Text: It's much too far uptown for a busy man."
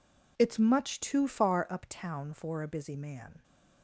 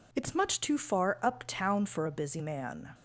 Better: neither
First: none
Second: none

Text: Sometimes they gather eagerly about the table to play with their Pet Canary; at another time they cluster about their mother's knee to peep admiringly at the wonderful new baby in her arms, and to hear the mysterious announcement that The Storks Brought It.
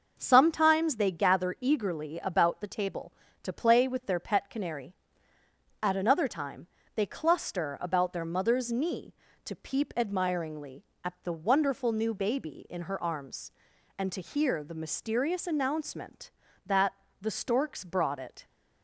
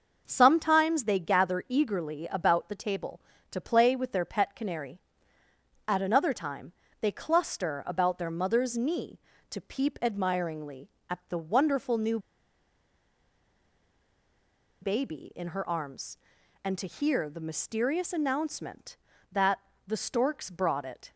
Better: first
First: pauses between "time" and "they"; slight; at 6.6 s; 0.28 s long // pauses between "that" and "The"; slight; at 16.9 s; 0.26 s long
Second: starts louder than the rest; noticeable; until 1.2 s; 6 dB // pauses between "time" and "they"; slight; at 6.7 s; 0.28 s long // pauses between "new" and "baby"; strong; at 12.1 s; 2.6 s long // pauses between "that" and "The"; slight; at 19.5 s; 0.26 s long

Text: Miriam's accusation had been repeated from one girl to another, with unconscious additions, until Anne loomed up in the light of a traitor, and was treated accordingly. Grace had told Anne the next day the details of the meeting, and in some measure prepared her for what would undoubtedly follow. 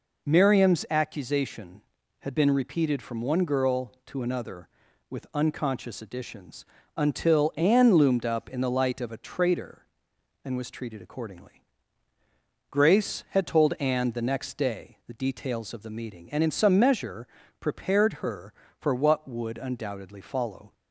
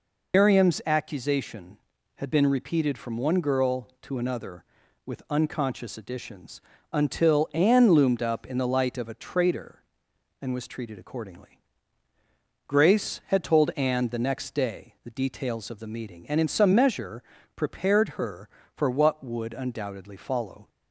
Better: first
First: pauses between "measure" and "prepared"; slight; at 17.2 s; 0.34 s long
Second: loses the start of "Miriam's"; at 0.3 s; 125 ms // pauses between "measure" and "prepared"; slight; at 17.2 s; 0.34 s long

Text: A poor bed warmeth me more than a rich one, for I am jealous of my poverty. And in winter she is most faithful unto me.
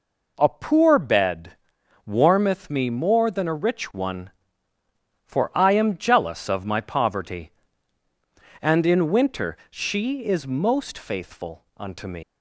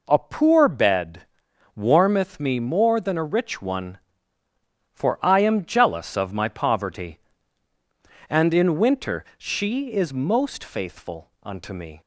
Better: second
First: pauses between "bed" and "warmeth"; noticeable; at 1.5 s; 0.54 s long // pauses between "faithful" and "unto"; slight; at 11.6 s; 0.16 s long // leaves "me" unfinished; at 12.2 s; 115 ms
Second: pauses between "bed" and "warmeth"; noticeable; at 1.2 s; 0.54 s long // pauses between "faithful" and "unto"; slight; at 11.2 s; 0.16 s long

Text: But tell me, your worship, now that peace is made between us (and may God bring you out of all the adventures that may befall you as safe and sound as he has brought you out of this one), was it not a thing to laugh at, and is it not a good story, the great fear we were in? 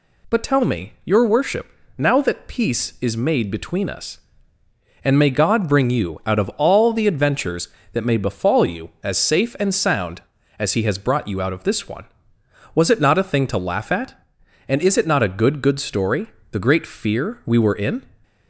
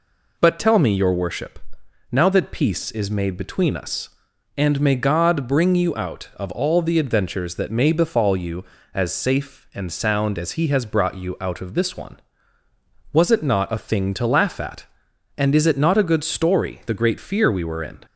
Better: second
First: says "good" twice; at 15.6 s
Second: none

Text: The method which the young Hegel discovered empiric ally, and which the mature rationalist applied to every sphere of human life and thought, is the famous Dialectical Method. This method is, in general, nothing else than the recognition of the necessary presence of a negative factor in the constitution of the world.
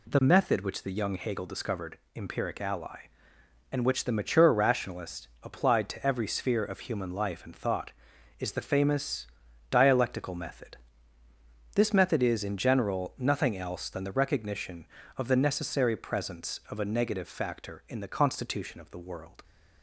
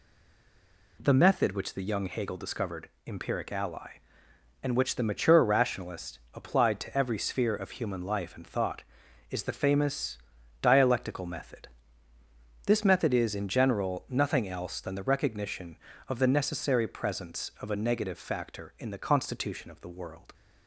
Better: first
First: pauses between "discovered" and "empiric"; slight; at 1.9 s; 0.18 s long // pauses between "rationalist" and "applied"; slight; at 5.2 s; 0.16 s long // pauses between "famous" and "Dialectical"; at 9.2 s; 0.42 s long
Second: stays silent before the first word; until 0.9 s; 0.9 s long // pauses between "discovered" and "empiric"; slight; at 2.8 s; 0.18 s long // pauses between "rationalist" and "applied"; slight; at 6.1 s; 0.16 s long // pauses between "famous" and "Dialectical"; at 10.1 s; 0.42 s long

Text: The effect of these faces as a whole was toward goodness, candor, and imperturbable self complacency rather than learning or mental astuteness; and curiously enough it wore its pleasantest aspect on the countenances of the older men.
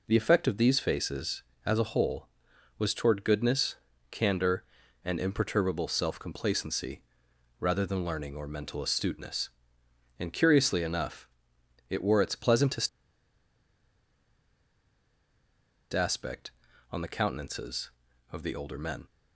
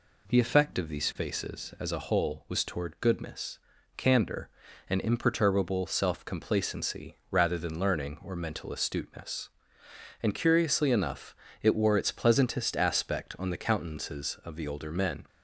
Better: second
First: pauses between "complacency" and "rather"; noticeable; at 7.0 s; 0.58 s long // pauses between "enough" and "it"; noticeable; at 11.2 s; 0.60 s long // pauses between "pleasantest" and "aspect"; strong; at 12.8 s; 3.0 s long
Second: pauses between "enough" and "it"; slight; at 11.3 s; 0.28 s long

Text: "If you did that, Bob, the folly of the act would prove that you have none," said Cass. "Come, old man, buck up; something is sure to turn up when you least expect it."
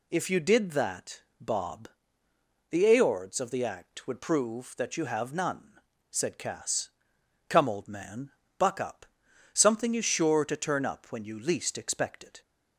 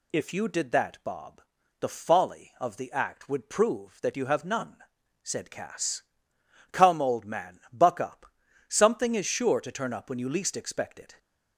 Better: second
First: says "aords" for "folly"; at 2.9 s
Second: none

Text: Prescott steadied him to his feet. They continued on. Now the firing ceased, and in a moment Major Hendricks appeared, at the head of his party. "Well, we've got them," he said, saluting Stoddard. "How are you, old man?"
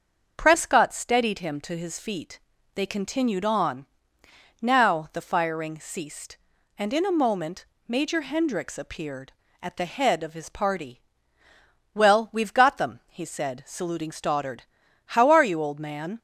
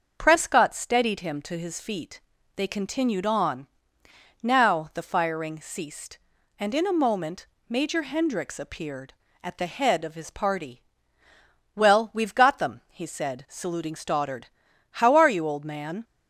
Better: neither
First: starts louder than the rest; until 1.3 s; 6.5 dB // pauses between "moment" and "Major"; slight; at 7.6 s; 0.24 s long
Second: starts louder than the rest; until 1.1 s; 6.5 dB // pauses between "moment" and "Major"; slight; at 7.4 s; 0.24 s long

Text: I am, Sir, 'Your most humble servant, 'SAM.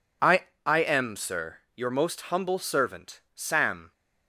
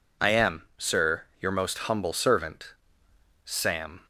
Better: second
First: says "I" twice; at 0.6 s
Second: none

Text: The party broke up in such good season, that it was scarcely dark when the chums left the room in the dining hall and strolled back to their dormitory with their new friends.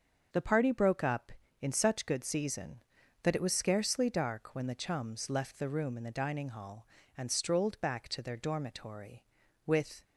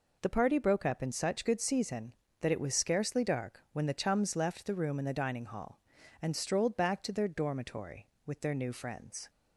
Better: second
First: starts louder than the rest; until 1.6 s; 6.5 dB // stops before "their new friends"; at 10.0 s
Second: none

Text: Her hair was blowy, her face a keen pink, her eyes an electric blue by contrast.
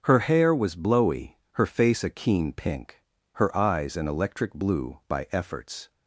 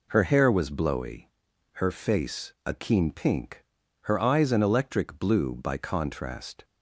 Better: second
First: starts louder than the rest; until 1.0 s; 6.5 dB // says "efforts" for "contrast"; at 5.3 s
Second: none

